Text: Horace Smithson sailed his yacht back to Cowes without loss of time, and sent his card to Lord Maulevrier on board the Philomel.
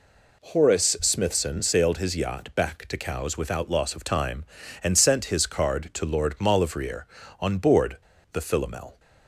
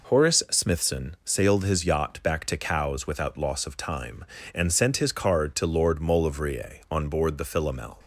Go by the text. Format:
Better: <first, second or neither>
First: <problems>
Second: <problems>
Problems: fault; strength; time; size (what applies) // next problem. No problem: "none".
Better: second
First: pauses between "board" and "the"; at 7.9 s; 0.36 s long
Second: none